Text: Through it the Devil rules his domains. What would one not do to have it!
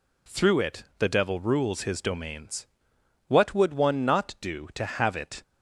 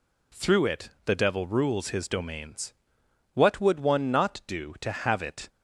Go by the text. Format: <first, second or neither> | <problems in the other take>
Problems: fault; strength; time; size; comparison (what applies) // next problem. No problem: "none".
neither | pauses between "it" and "the"; slight; the same in both